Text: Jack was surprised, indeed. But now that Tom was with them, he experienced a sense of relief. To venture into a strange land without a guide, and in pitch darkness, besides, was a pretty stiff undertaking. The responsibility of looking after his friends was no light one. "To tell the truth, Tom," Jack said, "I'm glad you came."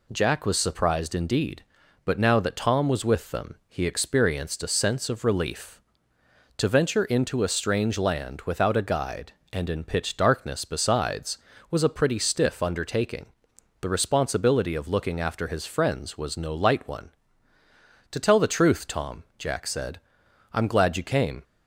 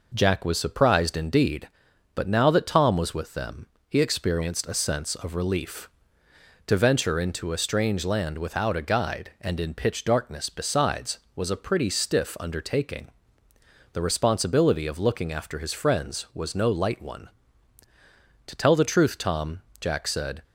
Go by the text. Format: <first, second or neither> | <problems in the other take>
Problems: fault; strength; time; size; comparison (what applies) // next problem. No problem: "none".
first | stops before "I'm glad you came"; at 20.4 s